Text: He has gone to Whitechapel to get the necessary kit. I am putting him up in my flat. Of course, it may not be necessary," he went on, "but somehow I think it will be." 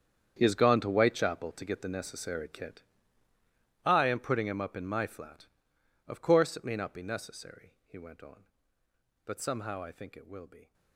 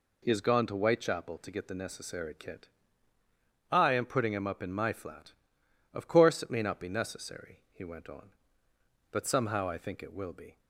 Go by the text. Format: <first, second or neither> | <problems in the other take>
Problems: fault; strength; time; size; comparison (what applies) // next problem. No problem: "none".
second | gets quieter; strong; throughout; 16 dB